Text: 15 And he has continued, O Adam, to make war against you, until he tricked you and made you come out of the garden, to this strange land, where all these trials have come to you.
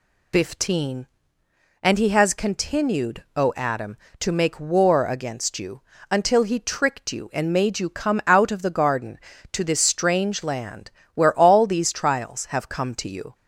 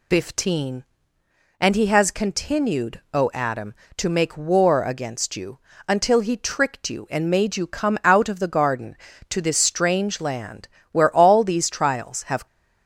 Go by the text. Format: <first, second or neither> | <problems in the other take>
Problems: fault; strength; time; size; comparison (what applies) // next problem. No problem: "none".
first | stops before "come to you"; at 12.4 s